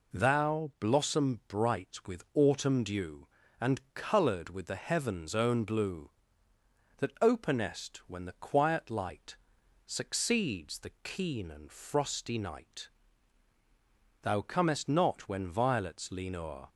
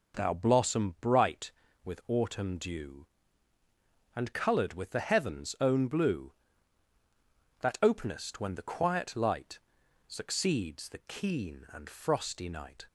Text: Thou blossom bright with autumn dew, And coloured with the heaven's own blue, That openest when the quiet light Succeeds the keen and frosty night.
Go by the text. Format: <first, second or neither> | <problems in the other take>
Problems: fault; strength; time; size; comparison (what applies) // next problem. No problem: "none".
second | pauses between "light" and "Succeeds"; noticeable; at 9.3 s; 0.50 s long; noticeable in the second // goes on to say "Thou comest not when violets lean O'er"; strong; from 14.2 s on; 2.4 s long